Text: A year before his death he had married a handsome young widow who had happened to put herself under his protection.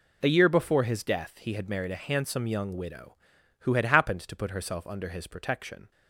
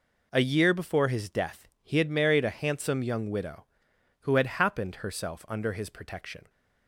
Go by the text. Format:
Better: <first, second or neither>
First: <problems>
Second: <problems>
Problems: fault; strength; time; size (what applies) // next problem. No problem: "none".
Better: first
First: none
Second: skips "to put"; at 4.9 s